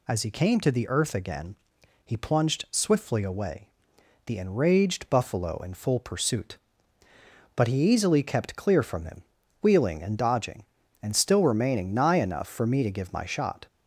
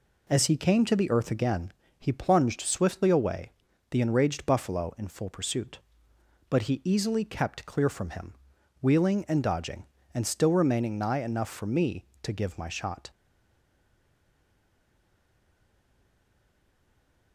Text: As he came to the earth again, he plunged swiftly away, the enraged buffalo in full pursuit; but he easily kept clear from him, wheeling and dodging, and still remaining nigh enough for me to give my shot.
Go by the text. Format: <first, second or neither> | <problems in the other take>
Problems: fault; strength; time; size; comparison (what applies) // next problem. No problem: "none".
first | stays silent after the last word; strong; from 13.0 s on; 4.3 s long